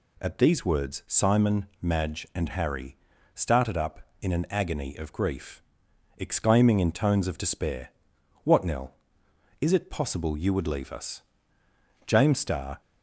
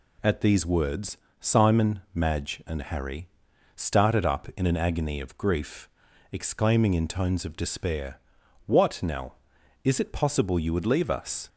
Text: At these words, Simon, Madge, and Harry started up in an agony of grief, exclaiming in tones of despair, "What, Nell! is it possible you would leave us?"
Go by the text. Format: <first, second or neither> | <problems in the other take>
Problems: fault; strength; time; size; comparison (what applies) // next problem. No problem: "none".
second | pauses between "Harry" and "started"; at 2.9 s; 0.38 s long; noticeable in the second // goes on to say "James Starr"; noticeable; from 12.0 s on; 0.74 s long